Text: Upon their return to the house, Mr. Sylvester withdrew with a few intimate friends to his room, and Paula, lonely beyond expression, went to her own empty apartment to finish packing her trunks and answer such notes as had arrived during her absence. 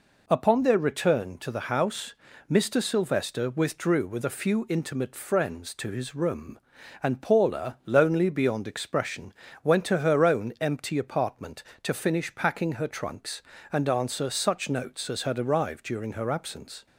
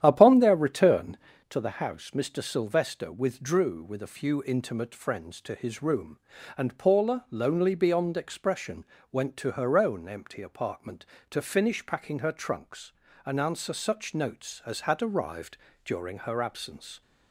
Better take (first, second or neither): first